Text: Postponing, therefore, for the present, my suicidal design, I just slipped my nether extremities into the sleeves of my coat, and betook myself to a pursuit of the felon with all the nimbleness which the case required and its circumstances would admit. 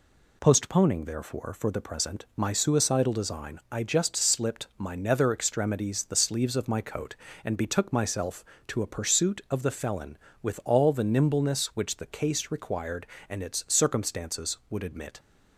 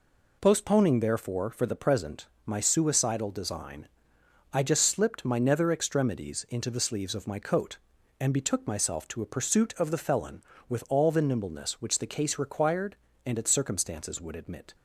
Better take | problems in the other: second | skips "into"; at 6.0 s

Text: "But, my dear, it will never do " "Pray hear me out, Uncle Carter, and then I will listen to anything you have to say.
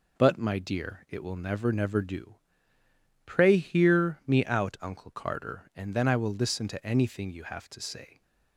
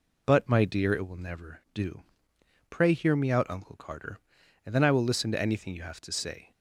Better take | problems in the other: second | says "never" twice; at 1.7 s

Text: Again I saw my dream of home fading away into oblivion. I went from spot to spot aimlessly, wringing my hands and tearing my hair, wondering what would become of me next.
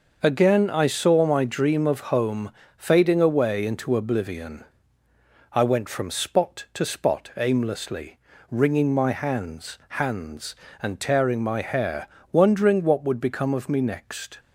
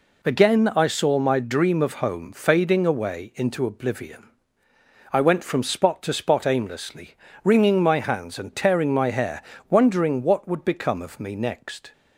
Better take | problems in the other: second | starts louder than the rest; noticeable; until 1.2 s; 6 dB // pauses between "home" and "fading"; slight; at 2.5 s; 0.26 s long // says "hands" twice; at 9.9 s

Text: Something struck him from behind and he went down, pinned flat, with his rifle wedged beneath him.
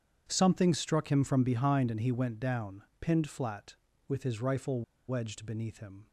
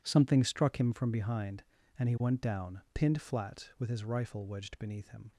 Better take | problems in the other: second | starts louder than the rest; strong; until 1.3 s; 8 dB // pauses between "rifle" and "wedged"; slight; at 4.8 s; 0.26 s long

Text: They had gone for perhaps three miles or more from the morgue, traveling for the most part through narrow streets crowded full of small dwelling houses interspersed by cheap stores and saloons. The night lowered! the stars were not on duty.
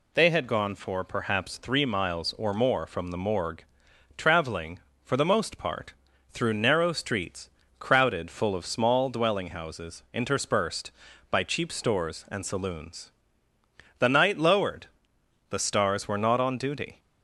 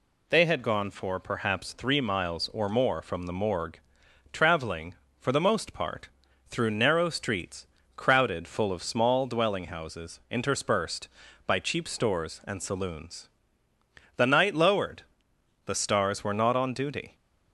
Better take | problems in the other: neither | pauses between "part" and "through"; the same in both // pauses between "streets" and "crowded"; slight; the same in both

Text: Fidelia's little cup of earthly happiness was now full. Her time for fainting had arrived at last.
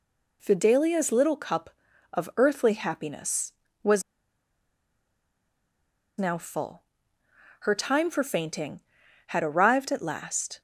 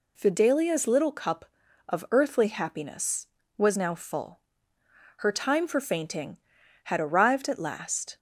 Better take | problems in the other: second | pauses between "was" and "now"; strong; at 4.0 s; 2.1 s long

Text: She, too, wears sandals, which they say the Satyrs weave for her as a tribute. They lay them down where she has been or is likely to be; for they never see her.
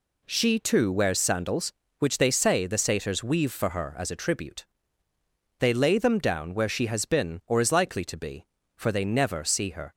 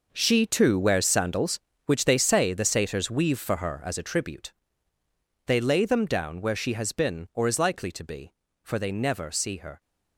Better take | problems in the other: first | gets quieter; strong; throughout; 12 dB

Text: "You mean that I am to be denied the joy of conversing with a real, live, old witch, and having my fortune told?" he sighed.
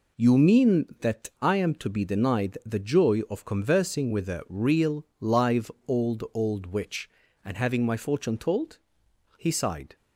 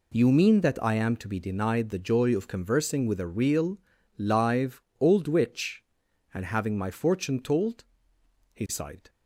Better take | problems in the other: second | says "old" twice; at 6.3 s

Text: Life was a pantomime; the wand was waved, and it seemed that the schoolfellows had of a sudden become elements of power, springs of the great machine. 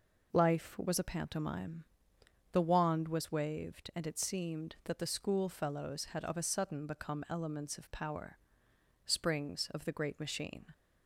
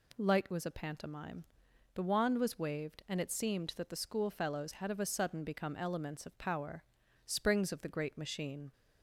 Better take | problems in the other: first | says "Light" for "Life"; at 0.1 s

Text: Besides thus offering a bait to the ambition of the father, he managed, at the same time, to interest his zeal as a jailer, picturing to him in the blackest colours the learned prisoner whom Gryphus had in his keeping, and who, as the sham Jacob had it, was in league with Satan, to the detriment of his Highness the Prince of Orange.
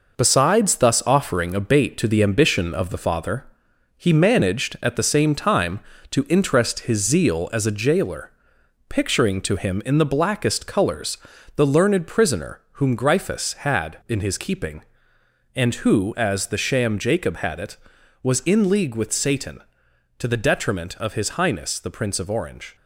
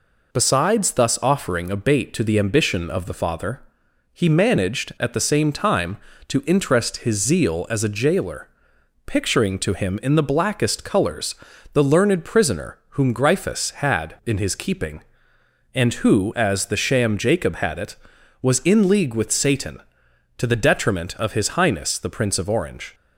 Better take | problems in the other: second | gets quieter; throughout; 6.5 dB // pauses between "colours" and "the"; at 11.1 s; 0.38 s long; also in the second

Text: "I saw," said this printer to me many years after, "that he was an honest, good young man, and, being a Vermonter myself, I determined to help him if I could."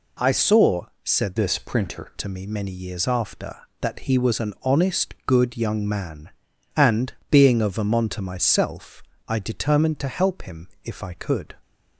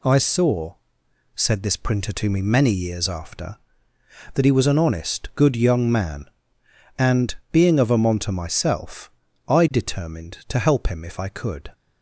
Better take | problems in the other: second | changes voice from "this" to "printer"; from 1.3 to 2.1 s; 0.8 s long // pauses between "him" and "if"; slight; at 10.6 s; 0.16 s long

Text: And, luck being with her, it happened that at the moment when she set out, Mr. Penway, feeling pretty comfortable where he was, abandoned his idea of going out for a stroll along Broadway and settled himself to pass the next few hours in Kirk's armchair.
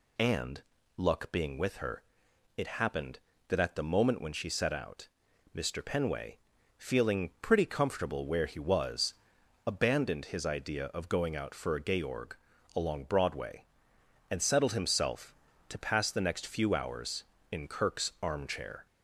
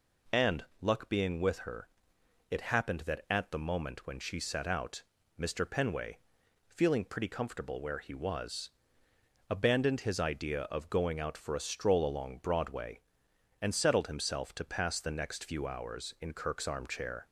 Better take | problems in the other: second | says "georg" for "stroll"; at 11.9 s

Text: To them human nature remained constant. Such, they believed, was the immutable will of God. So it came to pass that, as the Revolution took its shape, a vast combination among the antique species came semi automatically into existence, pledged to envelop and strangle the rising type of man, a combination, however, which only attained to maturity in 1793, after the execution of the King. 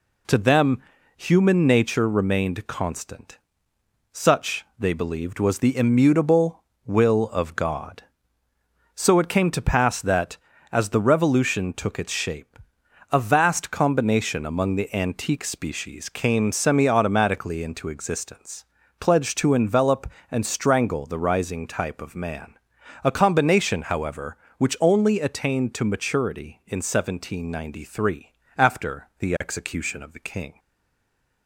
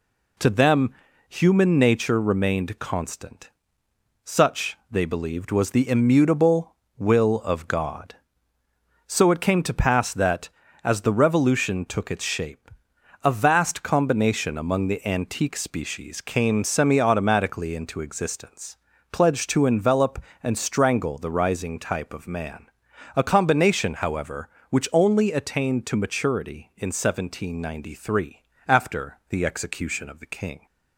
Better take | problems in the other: second | pauses between "them" and "human"; at 0.7 s; 0.38 s long; also in the second // stays silent after the last word; slight; from 30.5 s on; 0.9 s long

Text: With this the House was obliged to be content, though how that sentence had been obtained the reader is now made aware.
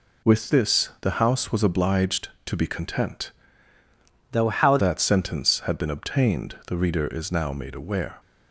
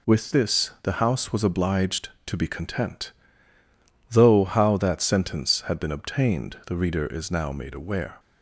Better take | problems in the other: second | changes voice from "though" to "how"; from 4.3 to 4.7 s; 0.4 s long

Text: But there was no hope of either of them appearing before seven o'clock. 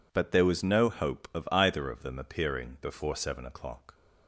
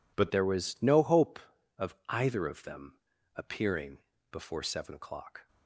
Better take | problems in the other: first | changes voice at "there"; from 0.3 s on; 5.1 s long // pauses between "them" and "appearing"; at 2.9 s; 0.38 s long // pauses between "appearing" and "before"; slight; at 3.9 s; 0.34 s long

